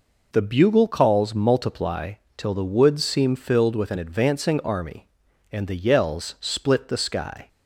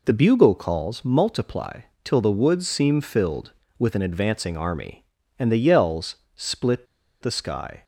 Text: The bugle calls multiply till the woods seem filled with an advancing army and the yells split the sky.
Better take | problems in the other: first | pauses between "multiply" and "till"; slight; at 1.8 s; 0.22 s long; slight in the first // pauses between "yells" and "split"; slight; at 6.1 s; 0.18 s long // pauses between "split" and "the"; at 6.8 s; 0.37 s long

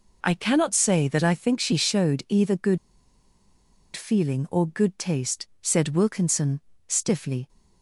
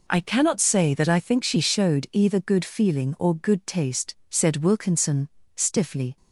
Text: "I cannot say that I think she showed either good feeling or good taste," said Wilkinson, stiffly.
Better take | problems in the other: second | pauses between "good" and "feeling"; at 2.7 s; 1.1 s long

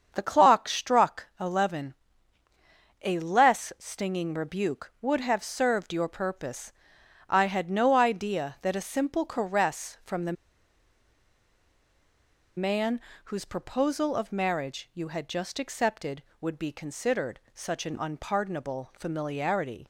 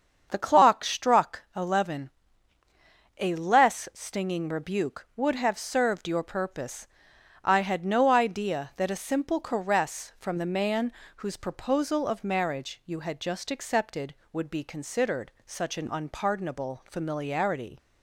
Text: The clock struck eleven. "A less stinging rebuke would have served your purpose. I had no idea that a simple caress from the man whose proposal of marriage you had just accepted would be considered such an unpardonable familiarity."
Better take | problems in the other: second | starts louder than the rest; strong; until 1.1 s; 7 dB; strong in the second // pauses between "the" and "man"; strong; at 10.3 s; 2.2 s long // pauses between "man" and "whose"; slight; at 12.9 s; 0.26 s long; slight in the second

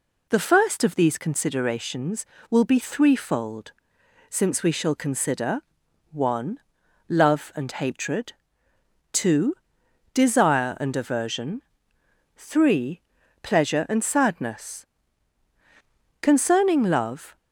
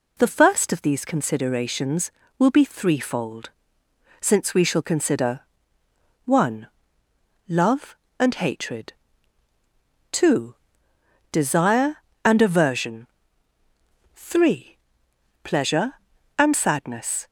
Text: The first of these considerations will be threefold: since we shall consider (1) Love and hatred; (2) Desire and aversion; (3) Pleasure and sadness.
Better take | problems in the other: second | goes on to say "Concerning love"; noticeable; from 16.2 s on; 1.1 s long

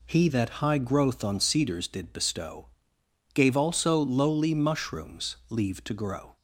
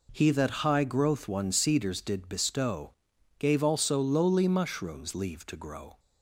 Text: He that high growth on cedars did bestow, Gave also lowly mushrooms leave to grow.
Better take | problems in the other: first | says "one" for "on"; at 1.2 s

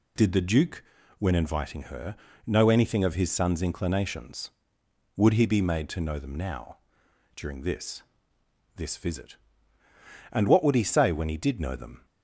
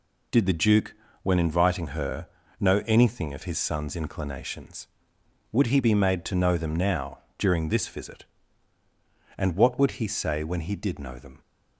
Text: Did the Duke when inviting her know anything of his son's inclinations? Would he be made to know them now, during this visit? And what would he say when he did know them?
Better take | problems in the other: second | pauses between "Duke" and "when"; slight; at 0.8 s; 0.36 s long; slight in the second // pauses between "her" and "know"; slight; at 2.1 s; 0.32 s long; slight in the second // says "this" twice; at 8.7 s

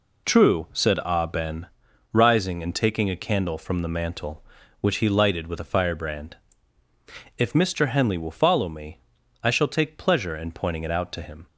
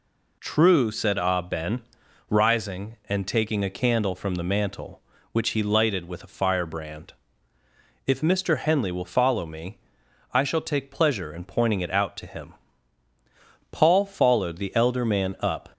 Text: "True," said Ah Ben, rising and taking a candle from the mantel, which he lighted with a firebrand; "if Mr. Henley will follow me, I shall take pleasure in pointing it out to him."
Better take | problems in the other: first | goes on to say "Paul followed the elder man up"; strong; from 13.7 s on; 1.9 s long

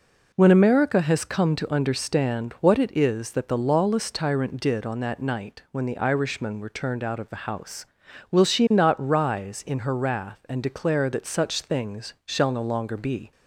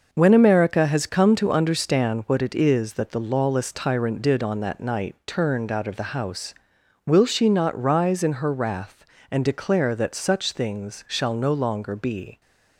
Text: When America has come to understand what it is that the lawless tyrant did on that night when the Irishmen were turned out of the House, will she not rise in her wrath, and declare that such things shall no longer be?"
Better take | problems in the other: first | skips "when the Irishmen were"; at 5.2 s

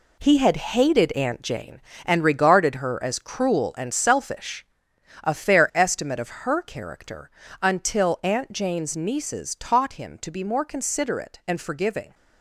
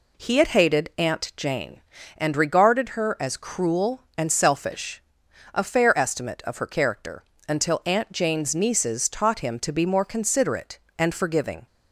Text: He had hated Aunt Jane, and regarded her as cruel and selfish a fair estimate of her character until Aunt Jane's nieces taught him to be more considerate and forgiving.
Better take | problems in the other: second | gets quieter; strong; throughout; 9 dB // pauses between "selfish" and "a"; noticeable; at 4.6 s; 0.60 s long; noticeable in the second // pauses between "character" and "until"; slight; at 7.3 s; 0.30 s long; slight in the second

